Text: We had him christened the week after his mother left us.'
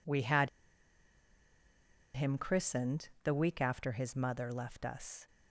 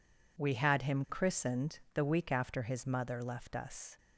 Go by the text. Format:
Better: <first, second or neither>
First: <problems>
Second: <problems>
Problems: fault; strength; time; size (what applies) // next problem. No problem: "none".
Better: second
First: pauses between "had" and "him"; strong; at 0.4 s; 1.6 s long // pauses between "christened" and "the"; slight; at 3.0 s; 0.16 s long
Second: pauses between "christened" and "the"; slight; at 1.7 s; 0.16 s long